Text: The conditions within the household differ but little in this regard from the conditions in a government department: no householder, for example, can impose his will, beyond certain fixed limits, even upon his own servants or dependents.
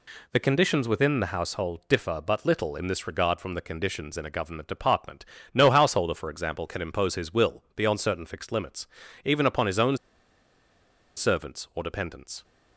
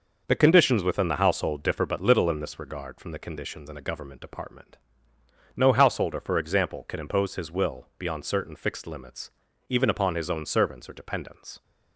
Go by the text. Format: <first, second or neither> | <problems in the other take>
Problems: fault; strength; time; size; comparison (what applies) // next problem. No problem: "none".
second | pauses between "own" and "servants"; at 9.9 s; 1.2 s long